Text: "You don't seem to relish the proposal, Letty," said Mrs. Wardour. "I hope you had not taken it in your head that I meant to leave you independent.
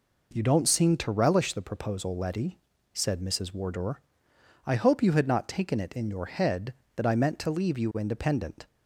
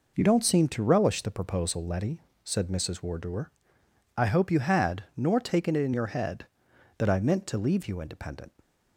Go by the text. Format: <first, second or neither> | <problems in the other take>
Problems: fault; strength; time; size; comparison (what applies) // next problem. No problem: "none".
first | says "nor" for "not"; at 5.1 s